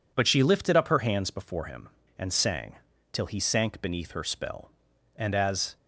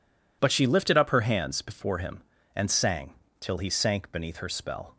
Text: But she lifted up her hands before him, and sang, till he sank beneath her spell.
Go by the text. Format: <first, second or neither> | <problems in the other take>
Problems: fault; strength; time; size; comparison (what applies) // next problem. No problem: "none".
second | goes on to say "And as"; from 5.1 s on; 0.60 s long